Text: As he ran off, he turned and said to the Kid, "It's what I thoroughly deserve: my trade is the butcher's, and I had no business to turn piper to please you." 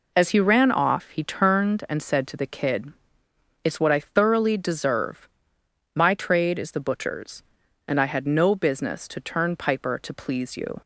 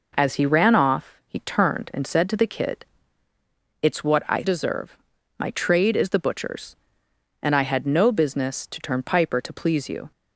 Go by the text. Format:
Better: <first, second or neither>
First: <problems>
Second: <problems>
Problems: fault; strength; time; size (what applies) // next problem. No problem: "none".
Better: first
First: none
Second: skips "thoroughly"; at 4.4 s